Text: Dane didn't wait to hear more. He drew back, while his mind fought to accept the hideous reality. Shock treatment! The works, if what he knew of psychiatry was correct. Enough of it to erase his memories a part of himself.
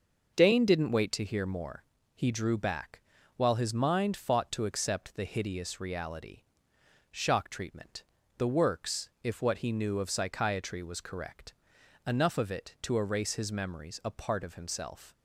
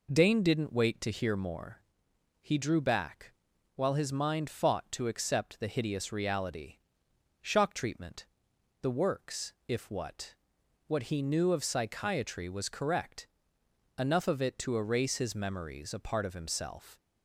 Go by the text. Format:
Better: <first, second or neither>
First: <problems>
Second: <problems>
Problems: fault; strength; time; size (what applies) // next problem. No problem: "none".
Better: first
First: none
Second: says "what" twice; at 10.8 s